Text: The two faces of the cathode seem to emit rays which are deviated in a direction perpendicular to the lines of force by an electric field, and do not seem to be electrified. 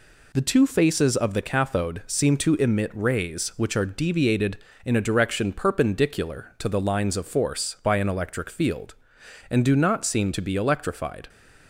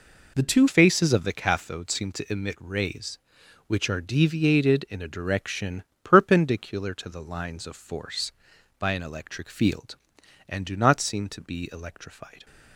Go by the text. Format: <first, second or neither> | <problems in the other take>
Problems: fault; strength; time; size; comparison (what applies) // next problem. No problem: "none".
first | changes voice at "faces"; from 0.6 s on; 11.8 s long // pauses between "direction" and "perpendicular"; slight; at 5.8 s; 0.20 s long